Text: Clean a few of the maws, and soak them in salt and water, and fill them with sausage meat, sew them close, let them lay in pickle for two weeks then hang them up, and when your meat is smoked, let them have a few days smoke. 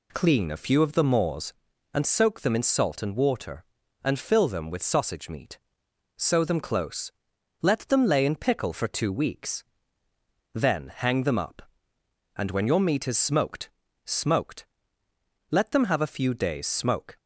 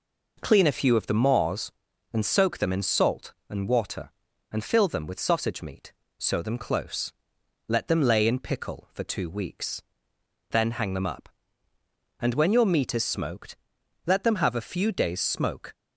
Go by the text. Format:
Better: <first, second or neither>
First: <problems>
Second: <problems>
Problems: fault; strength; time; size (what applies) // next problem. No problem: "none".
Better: second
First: pauses between "weeks" and "then"; noticeable; at 9.6 s; 0.90 s long // says "smoked" twice; at 14.0 s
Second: pauses between "weeks" and "then"; noticeable; at 9.8 s; 0.68 s long